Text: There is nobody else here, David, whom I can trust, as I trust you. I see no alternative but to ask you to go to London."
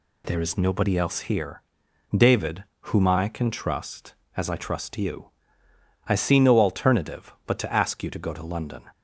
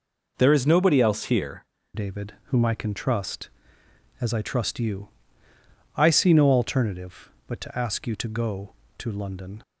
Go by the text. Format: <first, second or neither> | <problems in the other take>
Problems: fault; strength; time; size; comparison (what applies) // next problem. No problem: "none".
first | changes voice at "David"; from 1.9 s on; 7.7 s long